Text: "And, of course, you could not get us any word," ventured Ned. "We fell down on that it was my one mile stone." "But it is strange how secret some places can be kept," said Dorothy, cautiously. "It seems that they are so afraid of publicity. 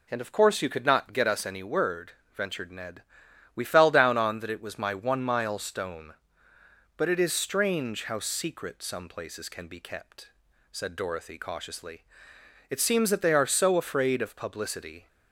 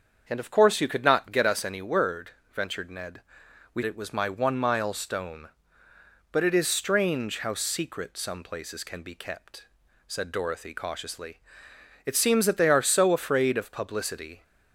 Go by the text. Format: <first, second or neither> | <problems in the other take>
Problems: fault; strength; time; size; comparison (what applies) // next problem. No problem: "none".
first | starts louder than the rest; until 1.2 s; 7 dB // skips "fell down on that"; at 3.8 s